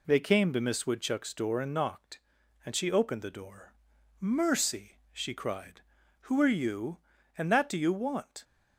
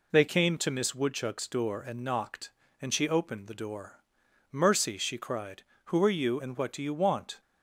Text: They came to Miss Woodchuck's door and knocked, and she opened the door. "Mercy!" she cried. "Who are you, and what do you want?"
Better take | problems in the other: second | says "that" for "what"; at 7.4 s

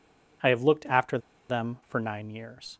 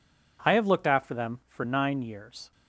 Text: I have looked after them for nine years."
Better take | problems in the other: second | pauses between "after" and "them"; slight; at 1.1 s; 0.30 s long

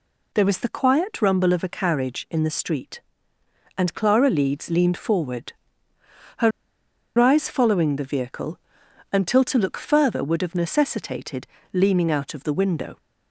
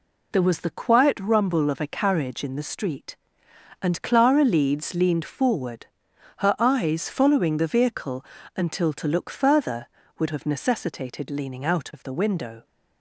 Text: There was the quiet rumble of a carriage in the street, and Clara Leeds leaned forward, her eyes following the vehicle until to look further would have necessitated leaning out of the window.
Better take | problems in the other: second | pauses between "her" and "eyes"; noticeable; at 6.5 s; 0.68 s long // pauses between "vehicle" and "until"; noticeable; at 8.5 s; 0.54 s long; slight in the second // pauses between "necessitated" and "leaning"; slight; at 11.4 s; 0.26 s long

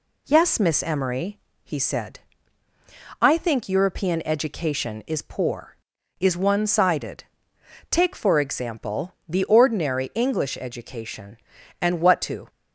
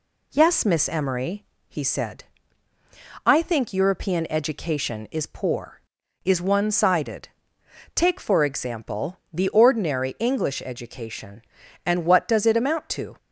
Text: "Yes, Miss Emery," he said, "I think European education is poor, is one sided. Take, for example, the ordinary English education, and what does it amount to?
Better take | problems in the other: second | skips "does it amount"; at 12.2 s

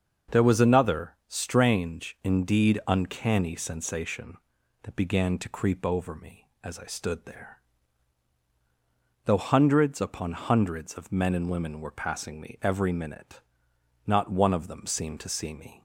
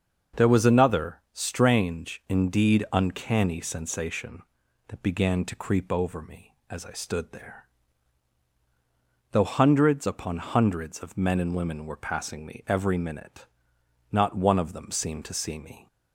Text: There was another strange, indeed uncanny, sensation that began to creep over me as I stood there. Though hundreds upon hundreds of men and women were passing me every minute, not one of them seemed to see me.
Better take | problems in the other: neither | starts louder than the rest; the same in both

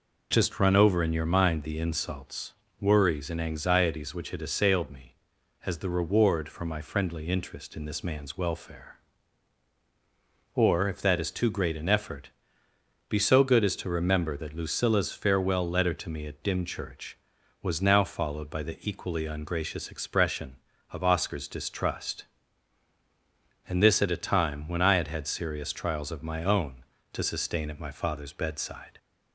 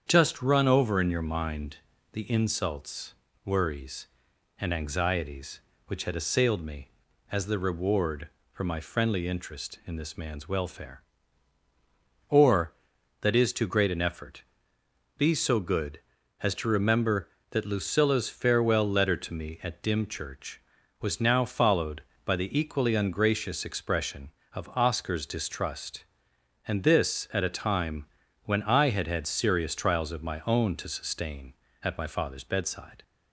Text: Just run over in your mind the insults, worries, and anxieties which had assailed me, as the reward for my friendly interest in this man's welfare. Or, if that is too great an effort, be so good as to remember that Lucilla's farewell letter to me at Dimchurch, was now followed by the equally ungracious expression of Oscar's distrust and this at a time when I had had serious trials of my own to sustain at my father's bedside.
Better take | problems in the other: first | starts louder than the rest; strong; until 1.0 s; 8 dB // pauses between "mind" and "the"; slight; at 1.7 s; 0.34 s long // skips "if"; at 12.9 s // pauses between "time" and "when"; at 28.0 s; 0.38 s long

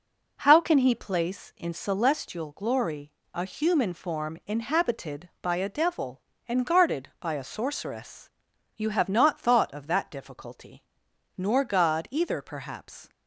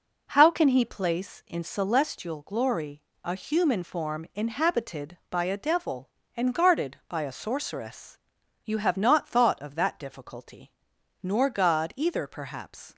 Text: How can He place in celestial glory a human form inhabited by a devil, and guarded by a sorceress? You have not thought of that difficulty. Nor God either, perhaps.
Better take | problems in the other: neither | pauses between "glory" and "a"; slight; the same in both

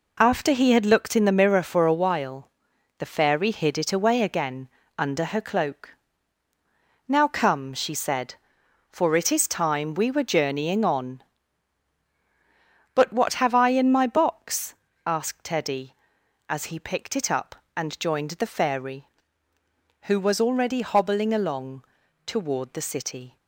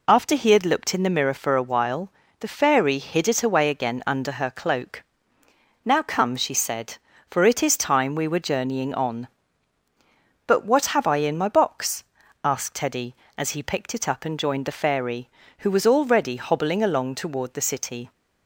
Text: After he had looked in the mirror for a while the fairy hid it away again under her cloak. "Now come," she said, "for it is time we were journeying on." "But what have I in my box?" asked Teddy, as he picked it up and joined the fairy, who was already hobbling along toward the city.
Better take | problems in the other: second | gets quieter; strong; throughout; 7.5 dB // pauses between "while" and "the"; noticeable; at 2.5 s; 0.48 s long; slight in the second // pauses between "again" and "under"; slight; at 4.6 s; 0.28 s long // pauses between "along" and "toward"; at 21.8 s; 0.42 s long

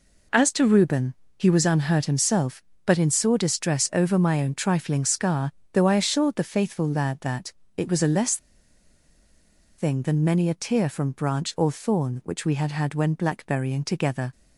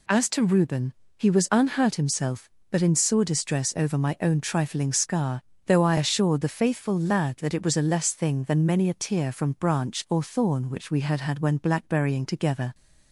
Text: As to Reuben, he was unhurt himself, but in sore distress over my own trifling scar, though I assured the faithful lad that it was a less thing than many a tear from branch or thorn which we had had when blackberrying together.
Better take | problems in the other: second | pauses between "that" and "it"; slight; at 7.5 s; 0.26 s long // pauses between "less" and "thing"; strong; at 8.3 s; 1.4 s long

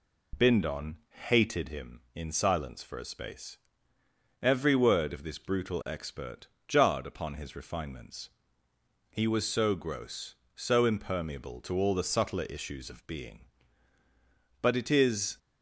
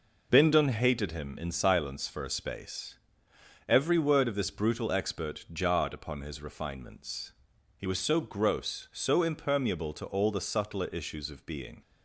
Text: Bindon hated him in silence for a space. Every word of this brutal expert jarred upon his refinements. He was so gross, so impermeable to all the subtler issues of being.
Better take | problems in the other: second | pauses between "Bindon" and "hated"; slight; at 0.9 s; 0.32 s long // pauses between "expert" and "jarred"; slight; at 6.4 s; 0.22 s long // goes on to say "But it is"; noticeable; from 14.6 s on; 0.76 s long

